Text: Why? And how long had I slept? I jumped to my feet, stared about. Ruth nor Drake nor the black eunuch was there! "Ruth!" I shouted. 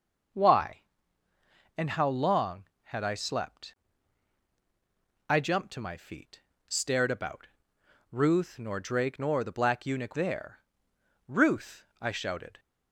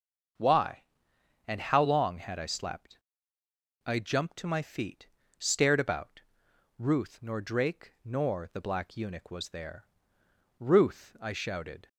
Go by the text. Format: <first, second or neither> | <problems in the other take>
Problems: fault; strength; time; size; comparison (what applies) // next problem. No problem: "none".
second | starts louder than the rest; until 2.3 s; 6 dB; also in the second // skips "was"; at 10.1 s